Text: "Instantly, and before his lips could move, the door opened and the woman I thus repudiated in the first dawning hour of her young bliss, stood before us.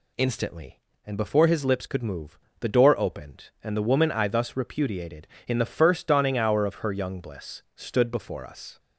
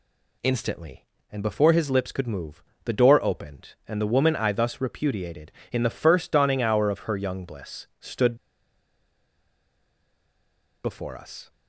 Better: first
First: none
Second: pauses between "stood" and "before"; strong; at 8.3 s; 2.4 s long

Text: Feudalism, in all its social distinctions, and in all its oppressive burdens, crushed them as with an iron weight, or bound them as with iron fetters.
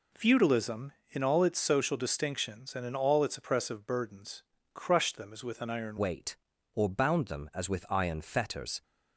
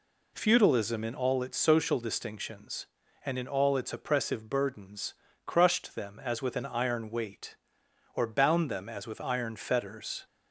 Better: second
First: changes voice at "weight"; from 5.9 s on; 2.9 s long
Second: none

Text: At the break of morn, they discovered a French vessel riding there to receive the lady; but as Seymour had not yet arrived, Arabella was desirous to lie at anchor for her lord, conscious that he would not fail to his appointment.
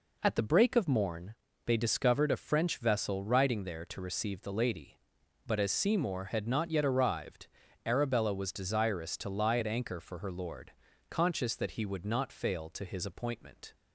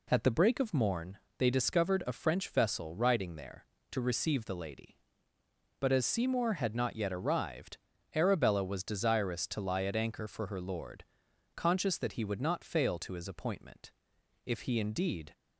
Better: first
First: none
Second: goes on to say "If he indeed"; noticeable; from 14.4 s on; 0.90 s long

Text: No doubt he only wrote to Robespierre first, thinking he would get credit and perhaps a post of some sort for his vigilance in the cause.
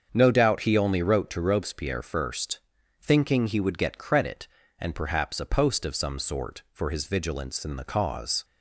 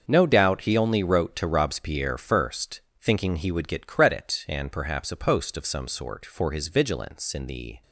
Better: first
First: starts louder than the rest; strong; until 1.1 s; 7 dB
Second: starts louder than the rest; until 1.0 s; 6.5 dB // stops before "cause"; at 7.8 s

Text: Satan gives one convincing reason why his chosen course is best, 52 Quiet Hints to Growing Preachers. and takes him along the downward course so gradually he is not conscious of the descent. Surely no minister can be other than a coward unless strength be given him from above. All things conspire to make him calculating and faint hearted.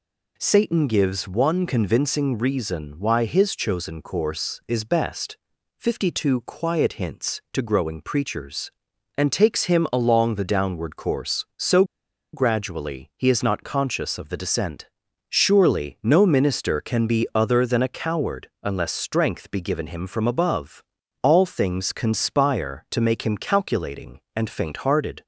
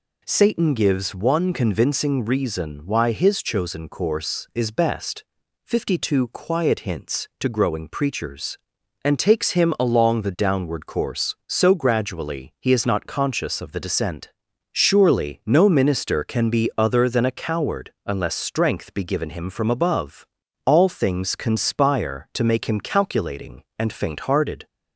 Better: second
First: pauses between "so" and "gradually"; noticeable; at 11.8 s; 0.49 s long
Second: none

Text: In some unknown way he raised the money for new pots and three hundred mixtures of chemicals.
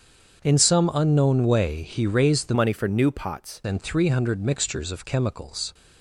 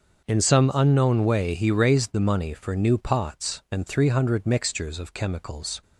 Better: second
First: starts louder than the rest; strong; until 1.4 s; 7 dB // changes voice from "money" to "pots"; from 2.5 to 3.6 s; 1.1 s long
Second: starts louder than the rest; until 1.2 s; 6.5 dB

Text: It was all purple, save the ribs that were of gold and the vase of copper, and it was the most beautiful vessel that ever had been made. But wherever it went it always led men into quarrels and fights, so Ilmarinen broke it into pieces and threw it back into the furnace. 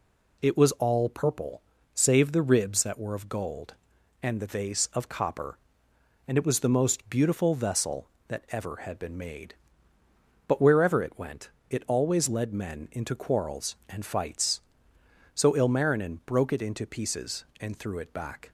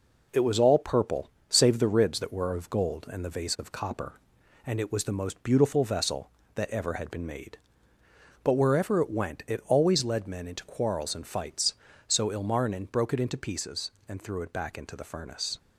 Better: second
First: pauses between "went" and "it"; slight; at 11.4 s; 0.20 s long // stops before "into the furnace"; at 18.4 s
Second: none

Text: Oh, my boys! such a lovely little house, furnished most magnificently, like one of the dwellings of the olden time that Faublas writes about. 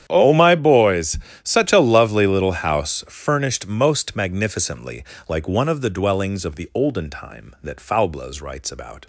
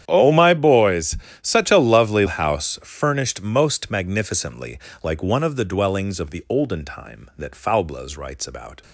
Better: first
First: starts louder than the rest; strong; until 1.0 s; 9.5 dB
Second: starts louder than the rest; strong; until 1.0 s; 10 dB // skips "little"; at 2.2 s

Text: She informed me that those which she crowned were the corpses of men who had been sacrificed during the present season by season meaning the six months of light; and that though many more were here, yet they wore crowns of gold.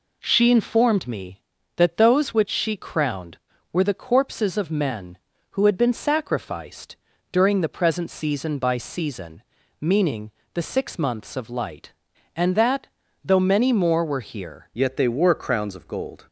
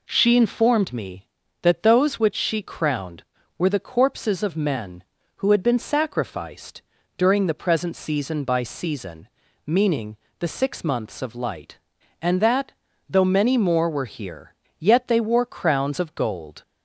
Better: second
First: pauses between "sacrificed" and "during"; slight; at 6.9 s; 0.36 s long // pauses between "season" and "meaning"; at 9.4 s; 0.40 s long // pauses between "meaning" and "the"; slight; at 10.3 s; 0.22 s long // pauses between "that" and "though"; at 12.8 s; 0.40 s long // changes voice at "yet"; from 14.7 s on; 1.5 s long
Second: pauses between "sacrificed" and "during"; slight; at 6.8 s; 0.36 s long // pauses between "season" and "meaning"; at 9.2 s; 0.40 s long // pauses between "meaning" and "the"; slight; at 10.1 s; 0.22 s long // pauses between "that" and "though"; at 12.6 s; 0.40 s long

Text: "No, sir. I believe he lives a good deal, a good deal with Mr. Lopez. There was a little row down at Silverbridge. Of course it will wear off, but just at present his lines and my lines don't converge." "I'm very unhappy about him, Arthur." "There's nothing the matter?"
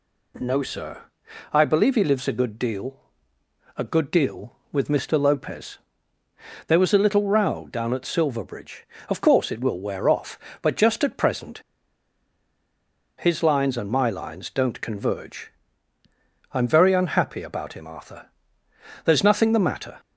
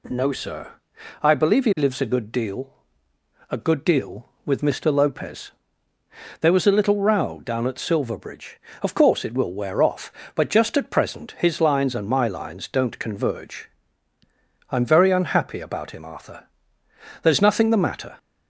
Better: second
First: pauses between "present" and "his"; strong; at 11.6 s; 1.5 s long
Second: none

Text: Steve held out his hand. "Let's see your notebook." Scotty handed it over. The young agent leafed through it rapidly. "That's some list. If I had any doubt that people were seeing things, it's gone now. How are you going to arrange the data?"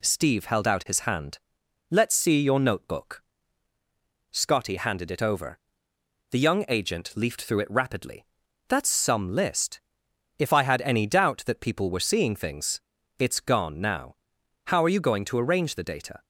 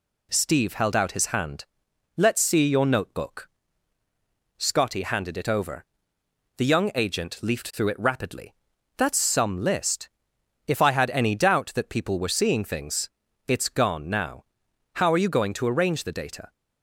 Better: neither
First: none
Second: none

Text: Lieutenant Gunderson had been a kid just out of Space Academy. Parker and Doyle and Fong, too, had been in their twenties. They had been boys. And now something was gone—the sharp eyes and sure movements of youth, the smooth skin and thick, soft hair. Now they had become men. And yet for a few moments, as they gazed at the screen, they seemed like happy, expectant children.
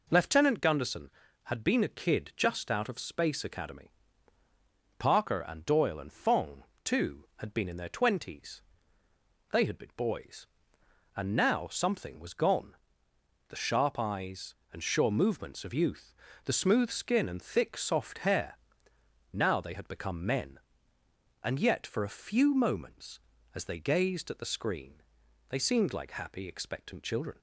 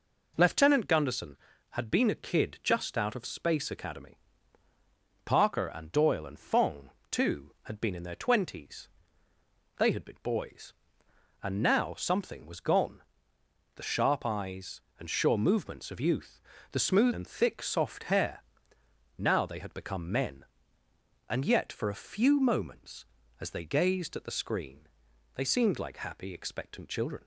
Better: first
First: none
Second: skips "skin"; at 17.1 s

